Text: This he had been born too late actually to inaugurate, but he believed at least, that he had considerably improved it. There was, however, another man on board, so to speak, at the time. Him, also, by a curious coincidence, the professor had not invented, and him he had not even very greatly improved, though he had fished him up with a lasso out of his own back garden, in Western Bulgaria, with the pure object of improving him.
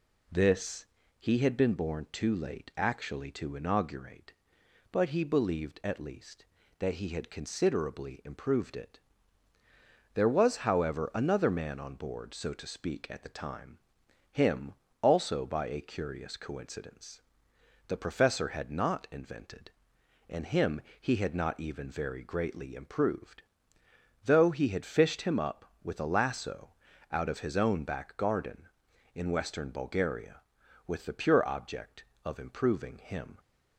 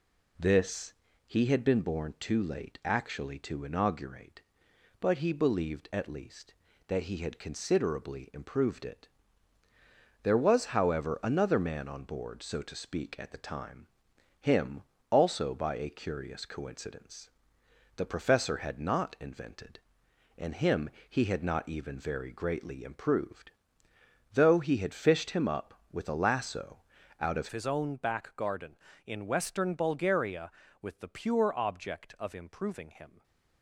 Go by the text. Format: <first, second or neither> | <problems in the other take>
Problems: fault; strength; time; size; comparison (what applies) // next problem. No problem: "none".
first | pauses between "This" and "he"; slight; at 0.9 s; 0.34 s long; slight in the first // pauses between "him" and "he"; slight; at 20.9 s; 0.18 s long; slight in the first // pauses between "lasso" and "out"; slight; at 26.8 s; 0.36 s long; slight in the first // changes voice at "his"; from 27.5 s on; 5.7 s long // stays silent after the last word; slight; from 33.0 s on; 0.6 s long